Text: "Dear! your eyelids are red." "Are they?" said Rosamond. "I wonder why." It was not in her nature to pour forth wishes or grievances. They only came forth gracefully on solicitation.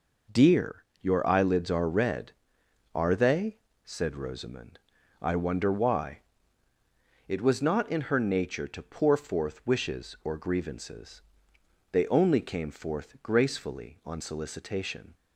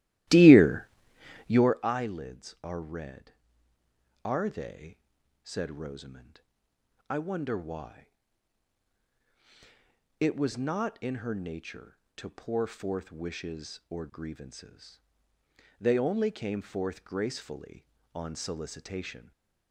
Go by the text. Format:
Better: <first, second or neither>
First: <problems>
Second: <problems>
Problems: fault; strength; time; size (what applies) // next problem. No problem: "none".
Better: first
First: none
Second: starts louder than the rest; strong; until 1.8 s; 15 dB // stays silent after the last word; slight; from 19.1 s on; 0.6 s long